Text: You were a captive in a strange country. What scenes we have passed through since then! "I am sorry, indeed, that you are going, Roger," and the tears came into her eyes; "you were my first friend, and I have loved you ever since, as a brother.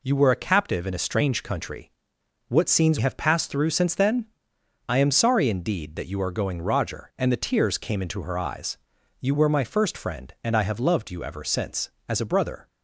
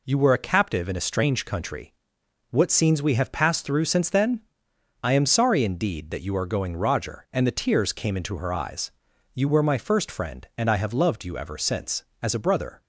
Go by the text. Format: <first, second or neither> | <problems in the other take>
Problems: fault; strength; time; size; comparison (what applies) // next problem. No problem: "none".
second | skips "we"; at 2.9 s